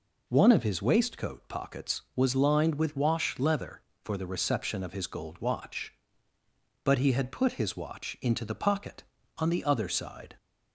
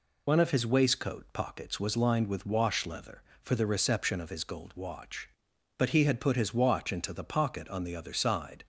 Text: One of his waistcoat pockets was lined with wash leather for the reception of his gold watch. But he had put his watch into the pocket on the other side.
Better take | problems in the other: first | loses the start of "One"; at 0.2 s; 50 ms

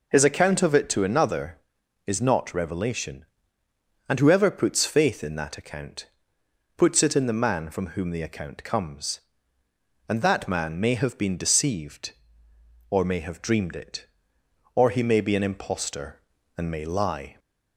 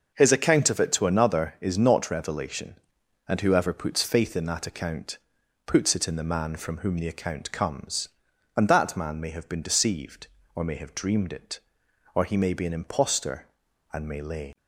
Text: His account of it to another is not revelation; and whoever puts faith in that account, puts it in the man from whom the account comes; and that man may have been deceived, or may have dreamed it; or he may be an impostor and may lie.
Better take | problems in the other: first | says "lay" for "lie"; at 14.2 s

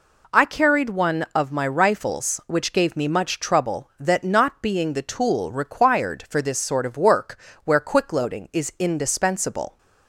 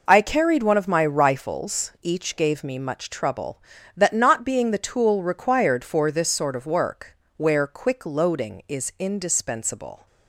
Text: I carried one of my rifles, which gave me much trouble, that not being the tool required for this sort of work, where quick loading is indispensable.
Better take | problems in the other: first | says "each" for "which"; at 2.0 s

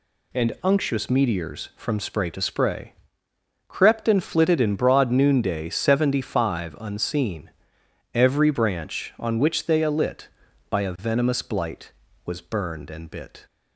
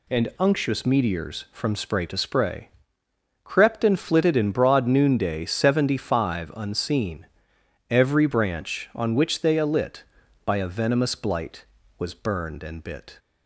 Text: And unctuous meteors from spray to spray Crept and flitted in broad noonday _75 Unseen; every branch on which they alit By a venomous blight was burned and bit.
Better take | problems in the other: neither | pauses between "spray" and "Crept"; noticeable; the same in both

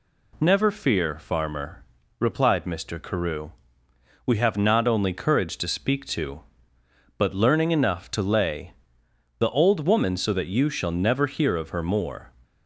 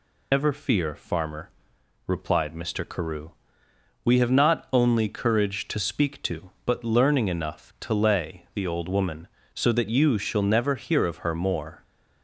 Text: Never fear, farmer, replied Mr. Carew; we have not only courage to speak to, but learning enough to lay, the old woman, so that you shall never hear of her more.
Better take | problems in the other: first | loses the start of "Never"; at 0.3 s; 150 ms

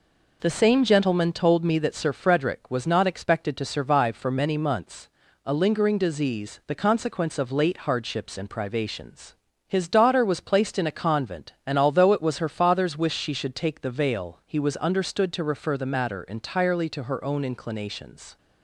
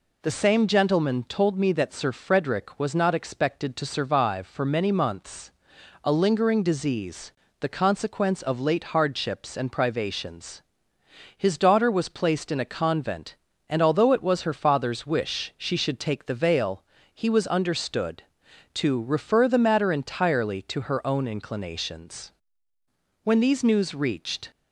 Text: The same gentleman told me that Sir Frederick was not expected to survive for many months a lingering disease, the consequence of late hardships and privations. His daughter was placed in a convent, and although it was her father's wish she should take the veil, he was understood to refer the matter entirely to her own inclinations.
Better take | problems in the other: first | pauses between "months" and "a"; noticeable; at 5.5 s; 0.50 s long; also in the first // goes on to say "When these news reached"; noticeable; from 23.2 s on; 1.2 s long

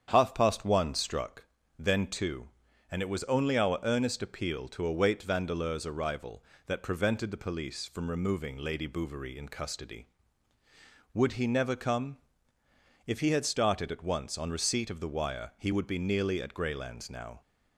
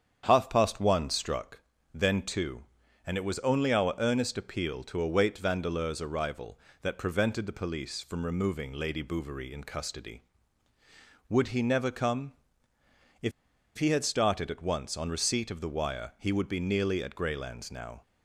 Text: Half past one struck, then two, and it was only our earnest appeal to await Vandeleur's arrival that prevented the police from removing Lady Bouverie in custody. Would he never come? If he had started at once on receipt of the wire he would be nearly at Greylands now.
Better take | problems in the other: first | starts louder than the rest; strong; until 1.2 s; 8 dB; strong in the first // pauses between "If" and "he"; noticeable; at 13.3 s; 0.46 s long

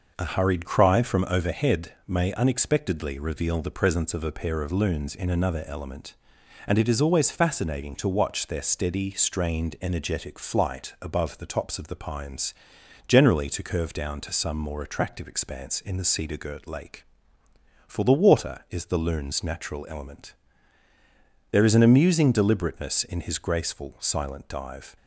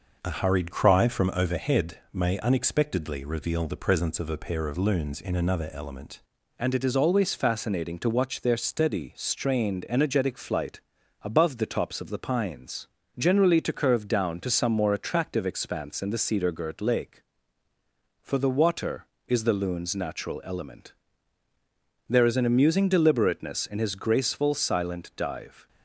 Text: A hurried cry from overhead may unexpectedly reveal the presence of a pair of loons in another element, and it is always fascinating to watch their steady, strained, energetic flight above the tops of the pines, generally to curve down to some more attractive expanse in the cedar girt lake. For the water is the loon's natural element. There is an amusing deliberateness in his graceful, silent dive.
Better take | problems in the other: first | changes voice at "and"; from 6.5 s on; 19.1 s long // pauses between "flight" and "above"; at 10.8 s; 0.40 s long

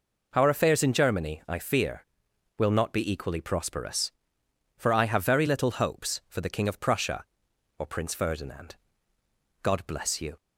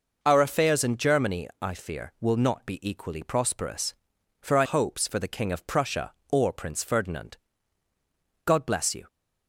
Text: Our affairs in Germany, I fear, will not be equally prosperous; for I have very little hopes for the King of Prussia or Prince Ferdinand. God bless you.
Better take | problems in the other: first | skips "have very little"; at 4.6 s

